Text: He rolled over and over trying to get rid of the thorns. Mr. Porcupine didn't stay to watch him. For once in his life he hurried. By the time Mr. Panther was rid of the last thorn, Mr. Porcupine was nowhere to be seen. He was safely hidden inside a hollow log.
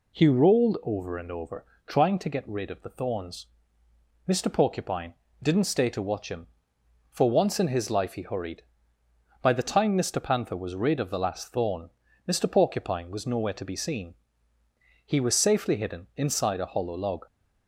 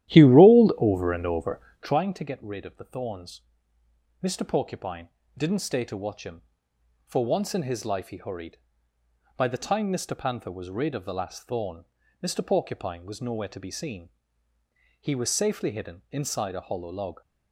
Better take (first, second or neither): first